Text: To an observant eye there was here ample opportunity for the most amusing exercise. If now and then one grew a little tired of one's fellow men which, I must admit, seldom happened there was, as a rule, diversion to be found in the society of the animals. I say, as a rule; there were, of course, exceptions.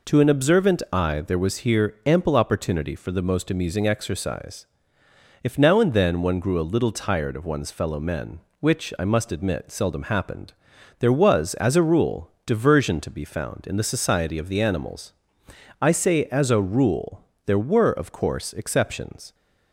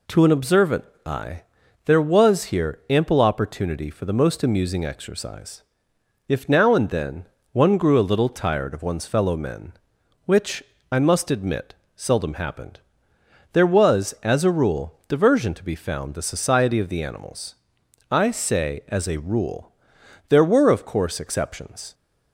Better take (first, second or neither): first